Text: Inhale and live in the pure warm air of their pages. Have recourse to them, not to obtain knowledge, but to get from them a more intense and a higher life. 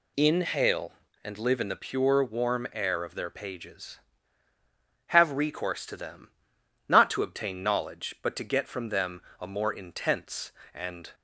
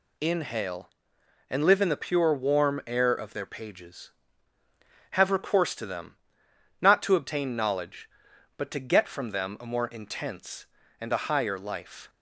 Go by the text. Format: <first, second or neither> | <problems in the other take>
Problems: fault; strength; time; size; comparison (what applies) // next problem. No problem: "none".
second | pauses between "them" and "a"; slight; at 9.2 s; 0.18 s long // stops before "a higher life"; at 11.1 s